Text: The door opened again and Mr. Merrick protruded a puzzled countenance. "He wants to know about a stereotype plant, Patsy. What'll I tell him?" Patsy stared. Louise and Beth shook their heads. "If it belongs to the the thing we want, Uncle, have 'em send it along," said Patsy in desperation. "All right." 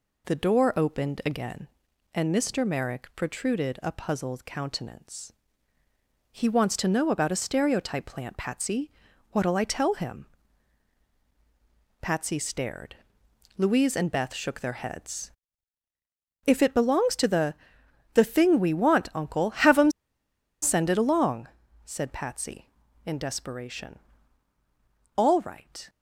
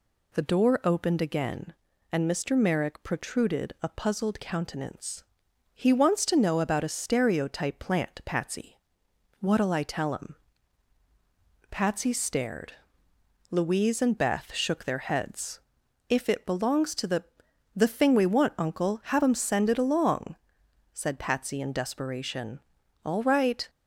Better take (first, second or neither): second